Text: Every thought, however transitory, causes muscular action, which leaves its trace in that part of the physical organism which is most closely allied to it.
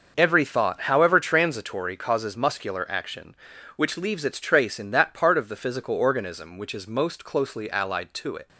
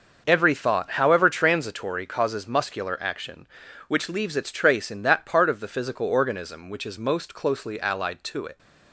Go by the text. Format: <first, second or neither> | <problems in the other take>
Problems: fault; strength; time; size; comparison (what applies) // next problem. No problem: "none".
neither | starts louder than the rest; noticeable; the same in both